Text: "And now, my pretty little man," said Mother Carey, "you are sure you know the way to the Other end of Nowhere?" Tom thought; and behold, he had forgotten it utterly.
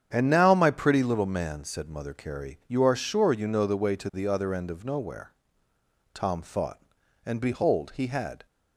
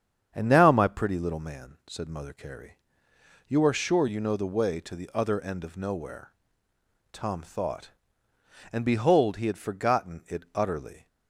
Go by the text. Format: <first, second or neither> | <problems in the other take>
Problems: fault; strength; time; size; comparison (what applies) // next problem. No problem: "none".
second | starts louder than the rest; strong; until 1.1 s; 8.5 dB; strong in the second // stops before "forgotten it utterly"; at 8.4 s